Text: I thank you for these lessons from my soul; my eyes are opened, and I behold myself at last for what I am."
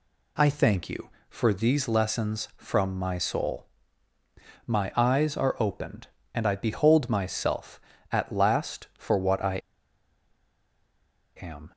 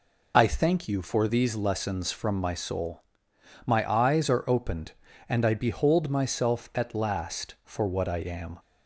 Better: second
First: pauses between "I" and "am"; strong; at 9.6 s; 1.7 s long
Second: none

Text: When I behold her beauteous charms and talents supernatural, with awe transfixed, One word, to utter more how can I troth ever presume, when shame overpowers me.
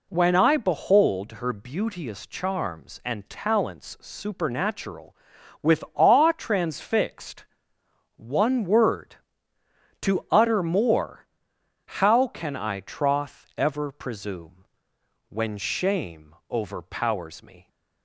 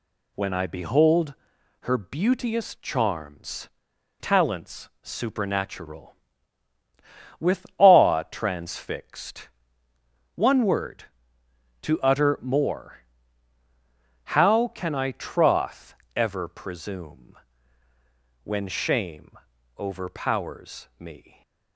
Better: first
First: pauses between "more" and "how"; noticeable; at 11.2 s; 0.74 s long // pauses between "shame" and "overpowers"; slight; at 16.3 s; 0.16 s long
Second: pauses between "behold" and "her"; noticeable; at 1.3 s; 0.46 s long // skips "and"; at 3.9 s // pauses between "more" and "how"; strong; at 12.9 s; 1.2 s long // pauses between "troth" and "ever"; slight; at 15.9 s; 0.22 s long // pauses between "shame" and "overpowers"; at 19.3 s; 0.40 s long

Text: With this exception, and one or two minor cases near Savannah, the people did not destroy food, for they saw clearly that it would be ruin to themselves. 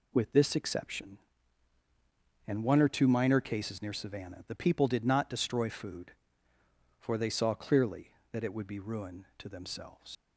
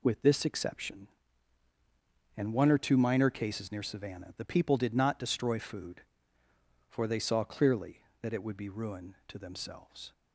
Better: second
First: leaves "themselves" unfinished; at 10.1 s; 80 ms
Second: none

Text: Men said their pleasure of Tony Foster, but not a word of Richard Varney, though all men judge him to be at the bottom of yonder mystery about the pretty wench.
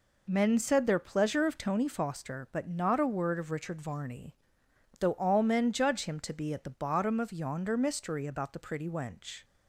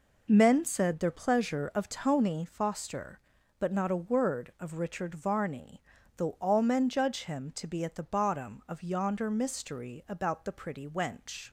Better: neither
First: none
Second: none

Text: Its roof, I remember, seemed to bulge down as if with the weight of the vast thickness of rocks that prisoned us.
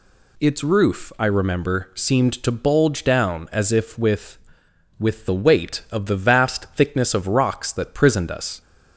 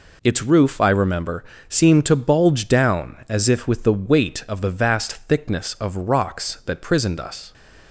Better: second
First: says "with" twice; at 4.9 s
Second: none

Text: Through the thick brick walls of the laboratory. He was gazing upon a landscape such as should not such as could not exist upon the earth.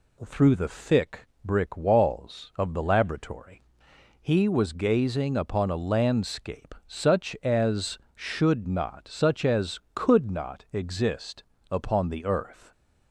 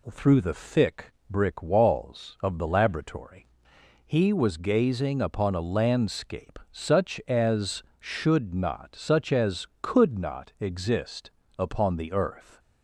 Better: neither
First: pauses between "thick" and "brick"; slight; at 1.2 s; 0.18 s long // pauses between "exist" and "upon"; slight; at 11.4 s; 0.26 s long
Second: pauses between "thick" and "brick"; slight; at 1.1 s; 0.18 s long // pauses between "exist" and "upon"; slight; at 11.3 s; 0.26 s long

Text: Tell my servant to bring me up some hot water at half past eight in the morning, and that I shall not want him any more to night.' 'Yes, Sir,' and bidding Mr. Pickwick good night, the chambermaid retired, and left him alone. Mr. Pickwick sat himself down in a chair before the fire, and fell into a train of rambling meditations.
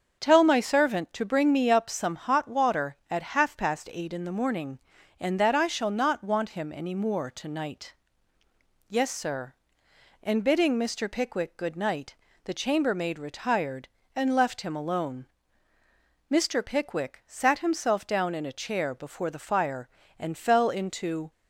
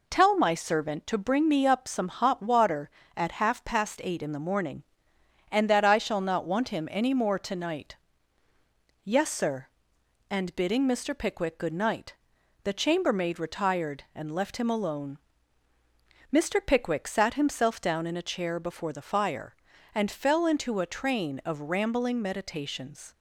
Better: second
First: starts louder than the rest; until 1.2 s; 6.5 dB // stops before "a train of rambling meditations"; at 21.3 s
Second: none

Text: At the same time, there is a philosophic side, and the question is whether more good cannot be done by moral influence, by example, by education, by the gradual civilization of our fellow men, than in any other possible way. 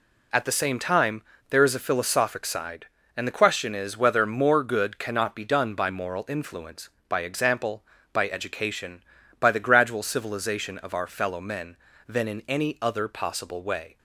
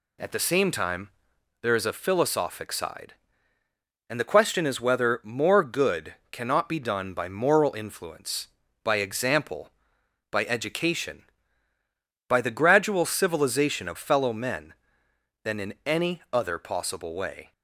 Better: first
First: none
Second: pauses between "good" and "cannot"; slight; at 6.1 s; 0.16 s long // skips "our"; at 13.9 s

